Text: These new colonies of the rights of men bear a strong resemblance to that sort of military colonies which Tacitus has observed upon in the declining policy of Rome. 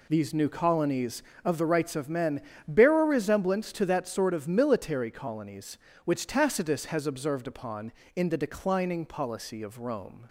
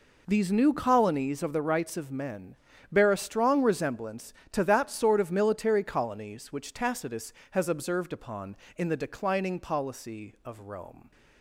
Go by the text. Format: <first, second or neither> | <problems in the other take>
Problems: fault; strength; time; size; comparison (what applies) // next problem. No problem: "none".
second | pauses between "men" and "bear"; slight; at 2.4 s; 0.26 s long; slight in the second // skips "strong"; at 3.0 s